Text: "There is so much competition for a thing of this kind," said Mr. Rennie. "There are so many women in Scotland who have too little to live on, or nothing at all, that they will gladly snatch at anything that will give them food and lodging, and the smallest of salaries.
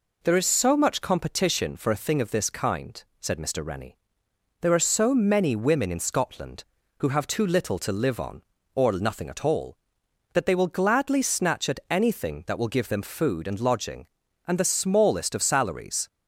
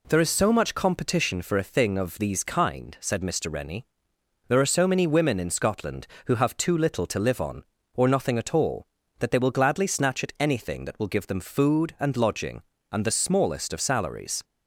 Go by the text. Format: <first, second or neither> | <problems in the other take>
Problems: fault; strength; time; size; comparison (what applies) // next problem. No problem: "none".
first | says "these" for "this"; at 2.1 s